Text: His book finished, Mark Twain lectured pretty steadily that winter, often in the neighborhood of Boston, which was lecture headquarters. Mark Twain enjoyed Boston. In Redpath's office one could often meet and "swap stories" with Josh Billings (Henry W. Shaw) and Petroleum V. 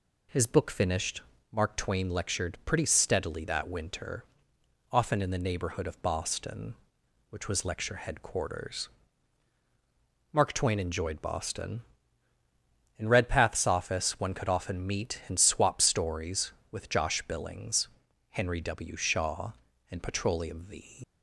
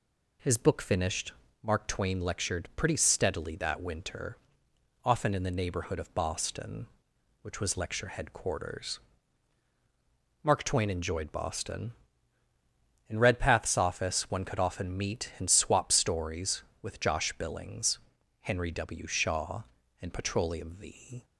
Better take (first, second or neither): second